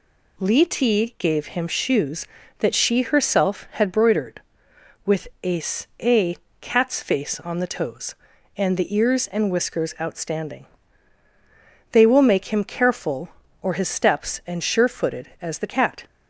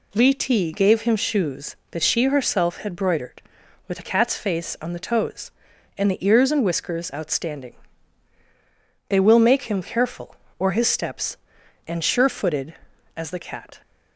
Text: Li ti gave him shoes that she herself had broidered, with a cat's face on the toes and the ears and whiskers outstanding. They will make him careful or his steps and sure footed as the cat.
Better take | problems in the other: second | says "a" twice; at 6.0 s

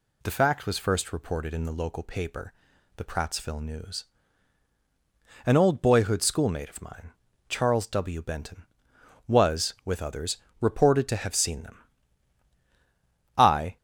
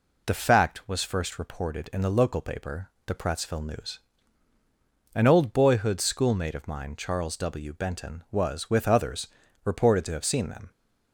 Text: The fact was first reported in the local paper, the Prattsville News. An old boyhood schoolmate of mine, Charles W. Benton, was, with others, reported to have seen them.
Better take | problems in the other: second | goes on to say "I"; slight; from 13.3 s on; 0.40 s long

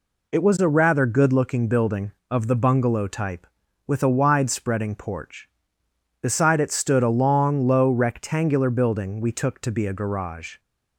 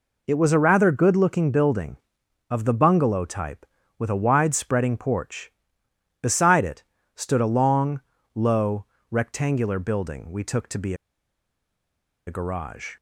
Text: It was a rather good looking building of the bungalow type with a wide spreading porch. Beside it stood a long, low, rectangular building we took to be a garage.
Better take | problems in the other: first | pauses between "it" and "stood"; slight; at 6.8 s; 0.30 s long // pauses between "be" and "a"; strong; at 10.9 s; 1.3 s long

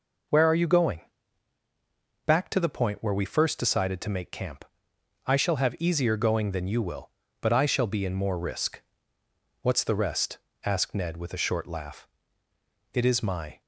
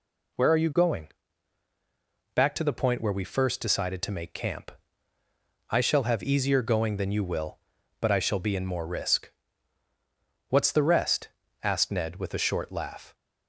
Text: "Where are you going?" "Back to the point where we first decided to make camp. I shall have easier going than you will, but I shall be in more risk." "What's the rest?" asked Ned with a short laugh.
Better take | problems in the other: second | goes on to say "It is my"; noticeable; from 12.9 s on; 0.66 s long

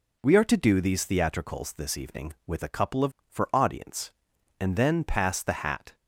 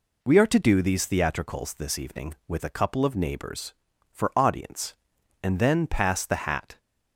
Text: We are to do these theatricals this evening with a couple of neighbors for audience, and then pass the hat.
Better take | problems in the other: second | skips "neighbors"; at 3.2 s

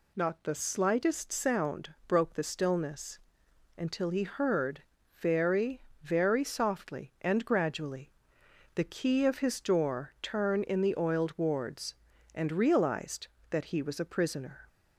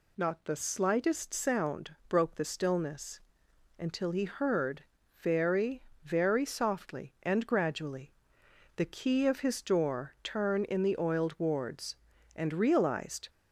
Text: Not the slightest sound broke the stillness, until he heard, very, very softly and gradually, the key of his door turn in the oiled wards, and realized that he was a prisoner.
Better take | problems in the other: first | stops before "that he was a prisoner"; at 13.2 s

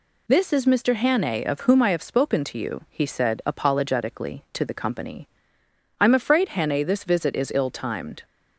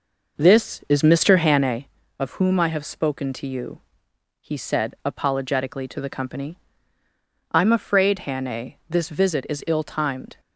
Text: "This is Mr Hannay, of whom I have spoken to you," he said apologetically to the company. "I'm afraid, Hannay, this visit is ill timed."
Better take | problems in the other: first | starts louder than the rest; noticeable; until 1.9 s; 5.5 dB

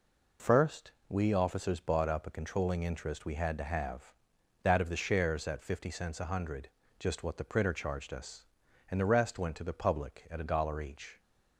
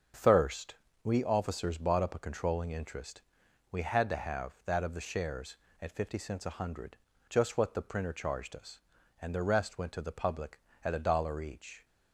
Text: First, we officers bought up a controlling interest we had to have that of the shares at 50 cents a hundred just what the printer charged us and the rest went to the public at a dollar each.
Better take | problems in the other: first | starts louder than the rest; until 1.4 s; 6.5 dB // says "Thirst" for "First"; at 0.1 s // pauses between "interest" and "we"; noticeable; at 3.2 s; 0.52 s long // pauses between "hundred" and "just"; slight; at 6.9 s; 0.34 s long; slight in the first

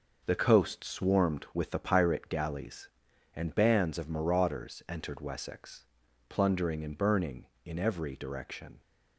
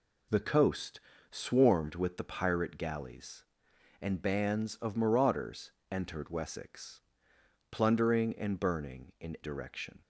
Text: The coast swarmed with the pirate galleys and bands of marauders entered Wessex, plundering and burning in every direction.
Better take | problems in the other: first | pauses between "coast" and "swarmed"; slight; at 0.9 s; 0.32 s long // pauses between "marauders" and "entered"; slight; at 5.7 s; 0.18 s long // skips "every"; at 9.3 s

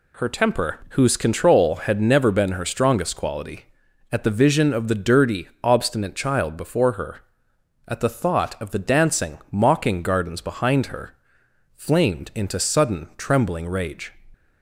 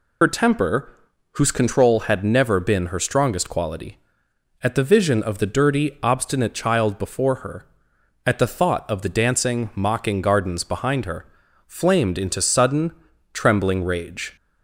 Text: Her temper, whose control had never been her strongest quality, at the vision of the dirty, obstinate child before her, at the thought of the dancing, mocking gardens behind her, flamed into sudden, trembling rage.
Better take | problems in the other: first | loses the start of "Her"; at 0.2 s; 50 ms

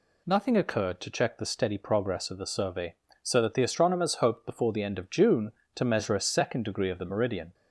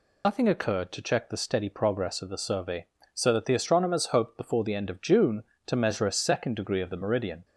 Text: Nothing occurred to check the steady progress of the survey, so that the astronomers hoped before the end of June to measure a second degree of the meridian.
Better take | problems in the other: first | loses the start of "Nothing"; at 0.2 s; 80 ms

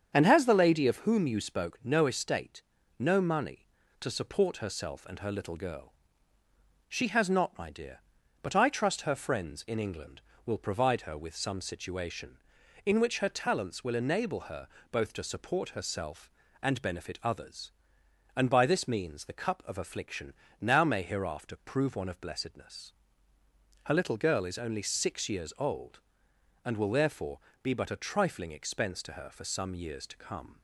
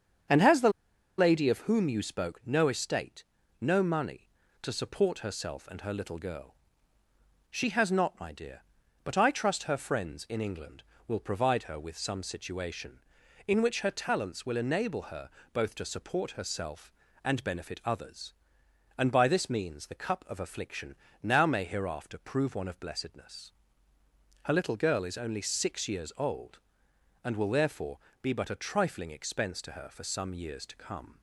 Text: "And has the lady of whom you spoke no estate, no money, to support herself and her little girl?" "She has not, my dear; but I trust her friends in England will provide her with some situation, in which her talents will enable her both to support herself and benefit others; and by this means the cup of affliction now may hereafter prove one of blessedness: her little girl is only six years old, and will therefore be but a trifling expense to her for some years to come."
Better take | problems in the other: first | starts louder than the rest; strong; until 1.7 s; 7.5 dB; strong in the first // pauses between "the" and "lady"; noticeable; at 0.6 s; 0.49 s long // pauses between "her" and "both"; slight; at 15.2 s; 0.24 s long; slight in the first // pauses between "affliction" and "now"; slight; at 20.9 s; 0.28 s long; slight in the first // pauses between "therefore" and "be"; slight; at 27.9 s; 0.24 s long; slight in the first

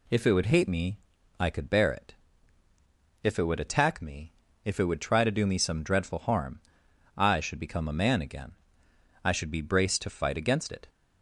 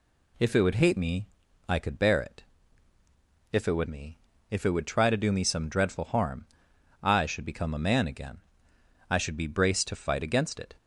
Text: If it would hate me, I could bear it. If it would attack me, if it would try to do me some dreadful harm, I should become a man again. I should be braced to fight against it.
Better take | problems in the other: first | skips "attack"; at 3.8 s

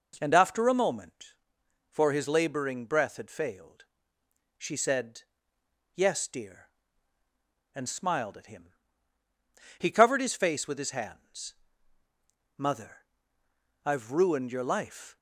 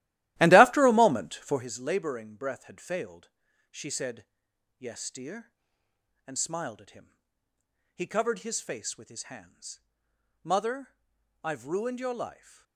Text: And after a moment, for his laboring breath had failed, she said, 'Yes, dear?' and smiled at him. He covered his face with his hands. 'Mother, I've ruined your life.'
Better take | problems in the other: first | starts louder than the rest; strong; until 1.7 s; 15.5 dB

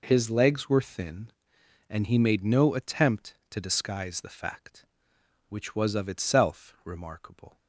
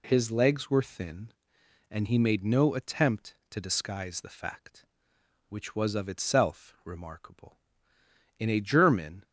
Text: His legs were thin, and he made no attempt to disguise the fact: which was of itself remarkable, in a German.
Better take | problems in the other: second | stops before "in a German"; at 7.5 s

